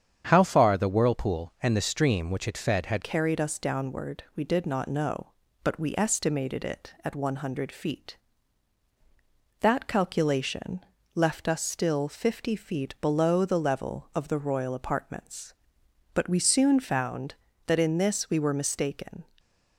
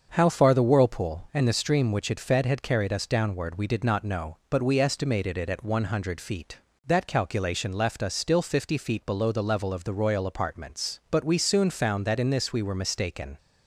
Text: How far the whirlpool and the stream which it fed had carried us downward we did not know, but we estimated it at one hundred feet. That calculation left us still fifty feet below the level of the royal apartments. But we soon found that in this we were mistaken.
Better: second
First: starts louder than the rest; strong; until 1.3 s; 8 dB // changes voice at "carried"; from 3.0 s on; 16.2 s long // pauses between "calculation" and "left"; slight; at 10.8 s; 0.34 s long // stays silent after the last word; slight; from 19.2 s on; 0.5 s long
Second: starts louder than the rest; until 1.1 s; 6.5 dB

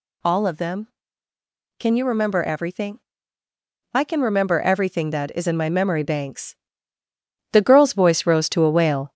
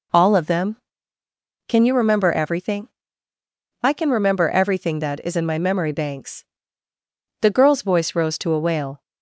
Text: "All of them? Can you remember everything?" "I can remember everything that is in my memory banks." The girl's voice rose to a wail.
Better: second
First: gets louder; slight; throughout; 3 dB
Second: none

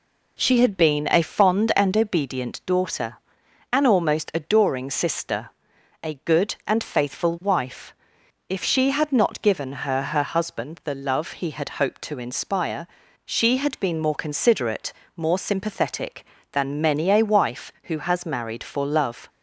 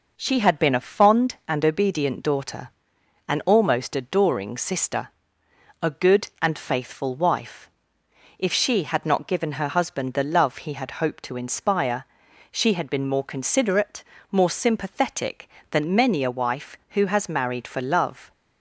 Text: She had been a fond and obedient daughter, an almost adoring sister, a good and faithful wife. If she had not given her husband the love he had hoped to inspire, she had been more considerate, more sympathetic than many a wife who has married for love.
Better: second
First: says "her" twice; at 10.0 s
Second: none

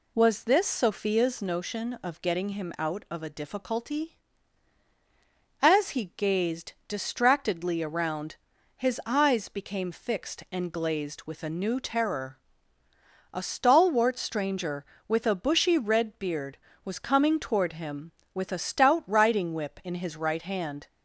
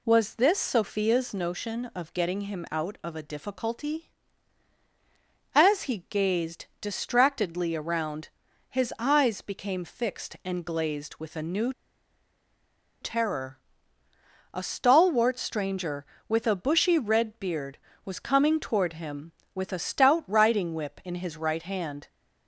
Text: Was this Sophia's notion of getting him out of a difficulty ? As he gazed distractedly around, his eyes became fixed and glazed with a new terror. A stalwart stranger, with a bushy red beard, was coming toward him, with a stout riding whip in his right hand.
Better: first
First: pauses between "gazed" and "distractedly"; slight; at 6.7 s; 0.16 s long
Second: pauses between "gazed" and "distractedly"; slight; at 6.6 s; 0.16 s long // pauses between "new" and "terror"; strong; at 11.7 s; 1.2 s long

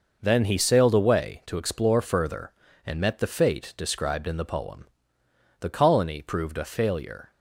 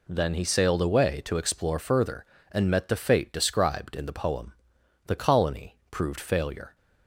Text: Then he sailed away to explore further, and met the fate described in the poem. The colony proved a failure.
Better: first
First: none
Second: skips "a"; at 6.1 s

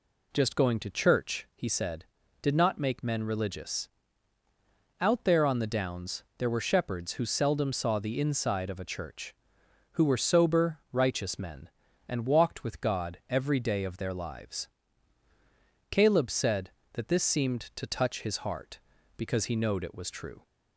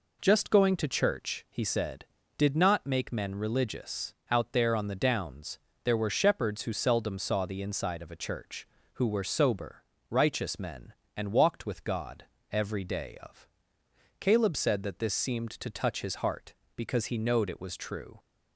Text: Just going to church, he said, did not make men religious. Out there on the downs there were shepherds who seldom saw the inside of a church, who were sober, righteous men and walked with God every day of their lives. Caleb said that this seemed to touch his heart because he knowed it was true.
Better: first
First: pauses between "downs" and "there"; slight; at 6.2 s; 0.16 s long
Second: pauses between "downs" and "there"; slight; at 5.5 s; 0.26 s long // pauses between "God" and "every"; slight; at 12.2 s; 0.26 s long // skips "their lives"; at 13.8 s

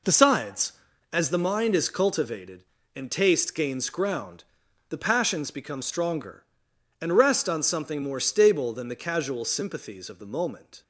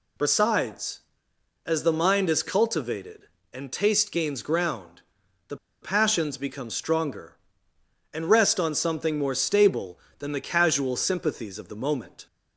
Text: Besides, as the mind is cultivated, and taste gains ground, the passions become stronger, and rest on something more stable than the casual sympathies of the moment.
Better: first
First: none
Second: pauses between "the" and "passions"; slight; at 5.5 s; 0.25 s long

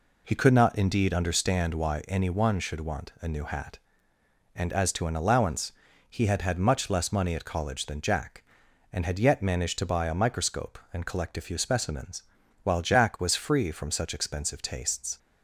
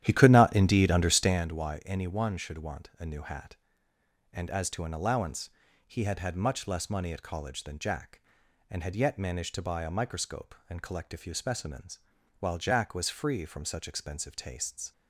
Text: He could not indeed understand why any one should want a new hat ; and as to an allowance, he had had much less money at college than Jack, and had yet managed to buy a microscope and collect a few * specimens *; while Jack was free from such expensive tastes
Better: first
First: none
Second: starts louder than the rest; strong; until 1.5 s; 11.5 dB

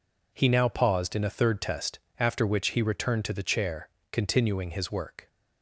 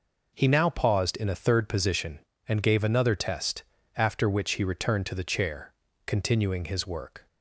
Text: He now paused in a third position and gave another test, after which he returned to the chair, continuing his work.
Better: second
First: skips "position and gave another"; at 1.6 s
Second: none

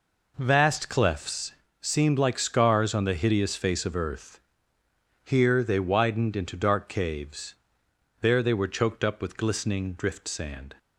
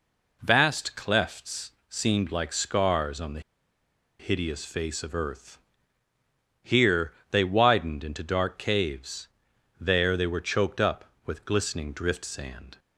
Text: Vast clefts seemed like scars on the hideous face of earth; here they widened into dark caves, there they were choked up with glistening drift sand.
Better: first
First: pauses between "clefts" and "seemed"; slight; at 1.5 s; 0.26 s long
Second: pauses between "clefts" and "seemed"; slight; at 1.7 s; 0.18 s long // pauses between "the" and "hideous"; noticeable; at 3.3 s; 0.79 s long // pauses between "here" and "they"; slight; at 7.1 s; 0.18 s long

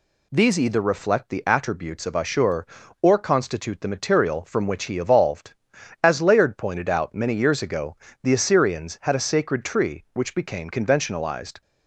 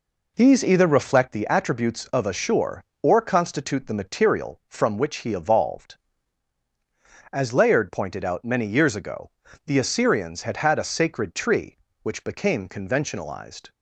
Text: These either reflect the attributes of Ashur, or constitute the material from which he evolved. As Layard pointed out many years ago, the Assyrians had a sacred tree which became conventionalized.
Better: first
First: none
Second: says "had" twice; at 10.5 s

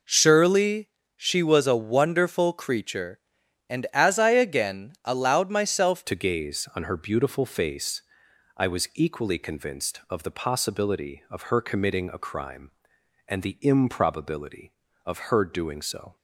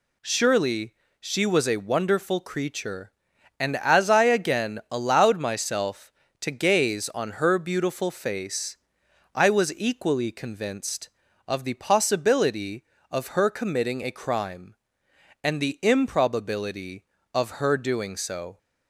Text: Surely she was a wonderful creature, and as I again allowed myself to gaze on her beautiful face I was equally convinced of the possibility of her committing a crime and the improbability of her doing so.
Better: second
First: pauses between "Surely" and "she"; slight; at 0.8 s; 0.26 s long // changes voice at "to"; from 6.0 s on; 10.1 s long // pauses between "face" and "I"; noticeable; at 8.0 s; 0.54 s long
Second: pauses between "Surely" and "she"; slight; at 0.9 s; 0.26 s long // pauses between "face" and "I"; noticeable; at 8.7 s; 0.58 s long

